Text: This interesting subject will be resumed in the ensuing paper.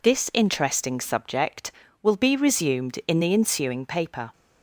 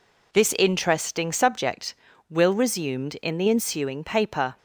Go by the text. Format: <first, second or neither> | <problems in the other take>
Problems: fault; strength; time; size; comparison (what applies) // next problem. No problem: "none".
first | skips "be"; at 2.5 s